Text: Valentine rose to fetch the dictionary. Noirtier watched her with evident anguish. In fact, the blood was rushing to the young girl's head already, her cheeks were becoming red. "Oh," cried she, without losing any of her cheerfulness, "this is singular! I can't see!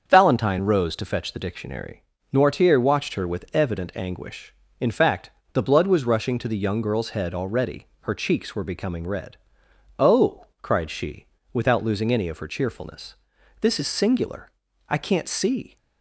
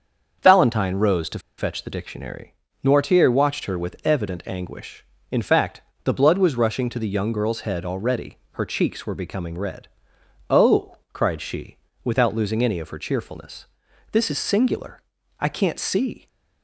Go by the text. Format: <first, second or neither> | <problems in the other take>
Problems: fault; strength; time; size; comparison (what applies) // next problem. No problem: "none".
first | starts louder than the rest; until 1.6 s; 7 dB; also in the first // pauses between "to" and "fetch"; slight; at 1.3 s; 0.19 s long